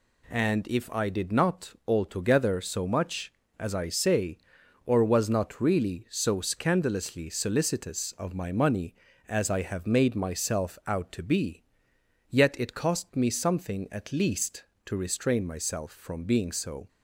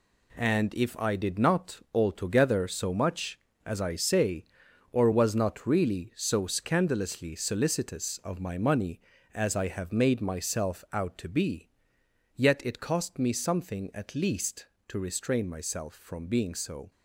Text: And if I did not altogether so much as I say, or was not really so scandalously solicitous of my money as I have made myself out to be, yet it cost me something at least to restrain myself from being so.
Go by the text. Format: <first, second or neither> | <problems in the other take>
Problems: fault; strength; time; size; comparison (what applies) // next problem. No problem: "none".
first | gets quieter; strong; throughout; 8 dB